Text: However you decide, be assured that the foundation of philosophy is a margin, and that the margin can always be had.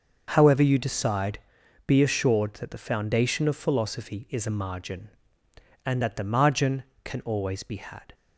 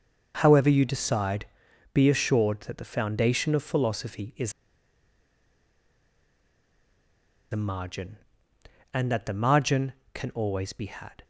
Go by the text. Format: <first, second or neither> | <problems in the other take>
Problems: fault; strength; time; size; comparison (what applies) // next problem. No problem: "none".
first | starts louder than the rest; until 1.4 s; 6 dB; also in the first // pauses between "is" and "a"; strong; at 4.5 s; 2.9 s long